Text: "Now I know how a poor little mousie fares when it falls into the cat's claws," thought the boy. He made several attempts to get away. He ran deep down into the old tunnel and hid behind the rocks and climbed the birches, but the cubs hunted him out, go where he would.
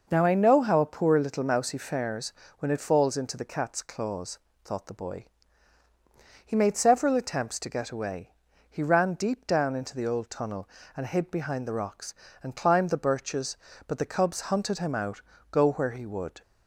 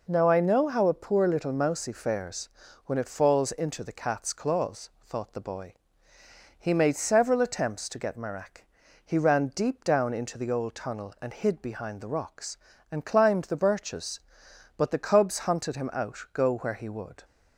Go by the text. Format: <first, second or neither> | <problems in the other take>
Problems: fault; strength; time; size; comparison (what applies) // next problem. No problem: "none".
first | pauses between "fares" and "when"; slight; at 2.4 s; 0.36 s long; slight in the first // says "marak" for "away"; at 8.1 s